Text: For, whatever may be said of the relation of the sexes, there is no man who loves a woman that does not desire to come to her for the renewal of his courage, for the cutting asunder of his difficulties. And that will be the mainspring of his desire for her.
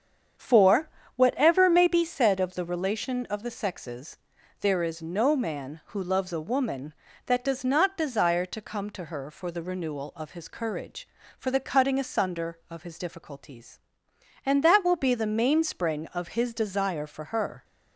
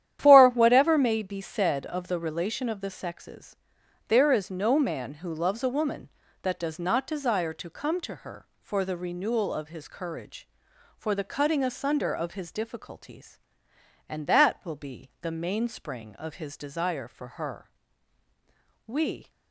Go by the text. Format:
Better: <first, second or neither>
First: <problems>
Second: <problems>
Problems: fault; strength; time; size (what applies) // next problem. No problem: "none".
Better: first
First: starts louder than the rest; strong; until 1.6 s; 7.5 dB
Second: starts louder than the rest; strong; until 1.2 s; 11 dB // goes on to say "We"; slight; from 18.8 s on; 0.44 s long